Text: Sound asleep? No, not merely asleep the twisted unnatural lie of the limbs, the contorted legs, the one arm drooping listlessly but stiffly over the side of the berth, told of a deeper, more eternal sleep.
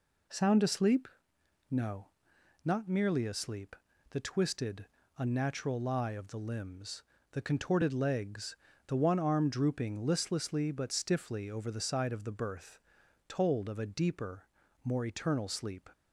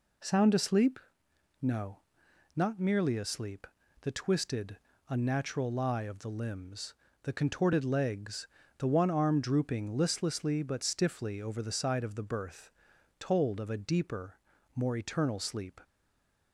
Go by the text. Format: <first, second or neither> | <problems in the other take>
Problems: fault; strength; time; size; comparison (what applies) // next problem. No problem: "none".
first | pauses between "asleep" and "the"; slight; at 3.6 s; 0.36 s long; slight in the first // pauses between "twisted" and "unnatural"; slight; at 4.7 s; 0.30 s long; slight in the first // stays silent after the last word; slight; from 15.8 s on; 0.7 s long